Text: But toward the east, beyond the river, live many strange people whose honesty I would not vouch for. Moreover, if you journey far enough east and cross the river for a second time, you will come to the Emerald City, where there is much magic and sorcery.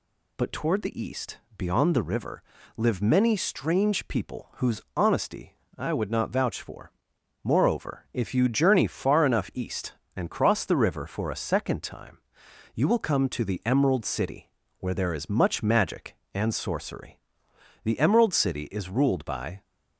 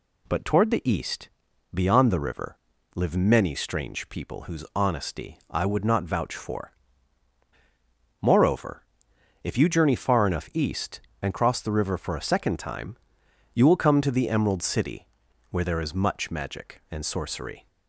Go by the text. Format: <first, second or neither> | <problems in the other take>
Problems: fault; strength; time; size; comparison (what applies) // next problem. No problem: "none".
second | pauses between "whose" and "honesty"; slight; at 4.8 s; 0.16 s long // pauses between "honesty" and "I"; slight; at 5.5 s; 0.22 s long // goes on to say "The Emerald City is ruled by"; strong; from 17.8 s on; 1.8 s long